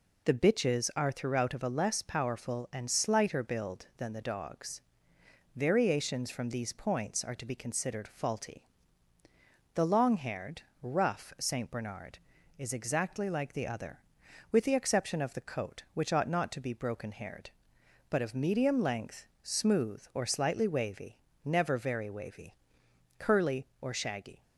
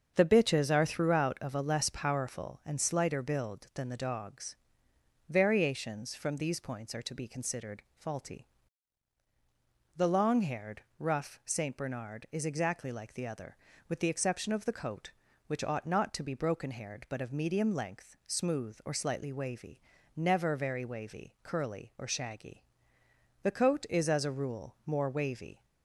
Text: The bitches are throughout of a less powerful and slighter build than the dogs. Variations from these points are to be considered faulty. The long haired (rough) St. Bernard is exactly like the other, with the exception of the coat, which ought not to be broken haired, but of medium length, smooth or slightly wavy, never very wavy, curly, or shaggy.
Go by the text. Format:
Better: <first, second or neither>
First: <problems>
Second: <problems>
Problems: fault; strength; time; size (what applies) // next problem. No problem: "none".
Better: first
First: none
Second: starts louder than the rest; until 1.1 s; 7 dB // goes on to say "The coat is as a rule more wavy"; strong; from 23.4 s on; 2.2 s long